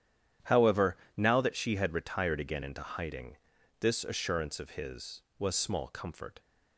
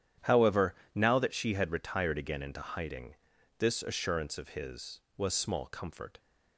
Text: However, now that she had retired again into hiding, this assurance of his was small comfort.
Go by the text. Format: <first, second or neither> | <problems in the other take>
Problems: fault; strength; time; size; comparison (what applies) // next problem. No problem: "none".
neither | starts louder than the rest; strong; the same in both